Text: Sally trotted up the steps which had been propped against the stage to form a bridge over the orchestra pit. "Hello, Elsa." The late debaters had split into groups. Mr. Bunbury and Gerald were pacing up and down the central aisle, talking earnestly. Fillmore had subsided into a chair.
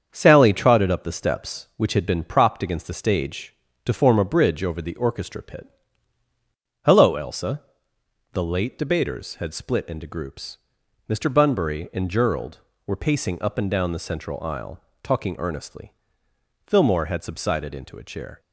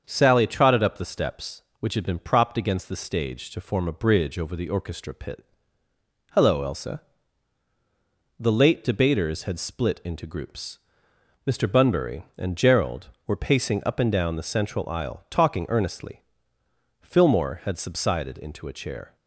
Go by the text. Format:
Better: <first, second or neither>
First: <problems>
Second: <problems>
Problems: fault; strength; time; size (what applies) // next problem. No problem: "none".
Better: neither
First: starts louder than the rest; strong; until 1.1 s; 7.5 dB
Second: starts louder than the rest; until 1.0 s; 7 dB